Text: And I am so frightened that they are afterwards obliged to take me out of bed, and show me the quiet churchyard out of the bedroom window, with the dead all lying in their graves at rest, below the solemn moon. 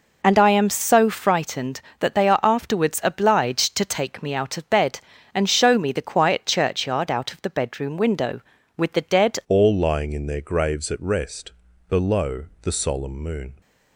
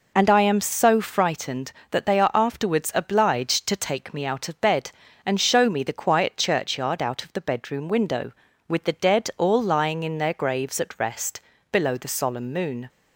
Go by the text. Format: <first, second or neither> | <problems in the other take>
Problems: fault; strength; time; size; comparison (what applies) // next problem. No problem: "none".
second | changes voice at "all"; from 9.4 s on; 4.2 s long // pauses between "below" and "the"; slight; at 12.4 s; 0.18 s long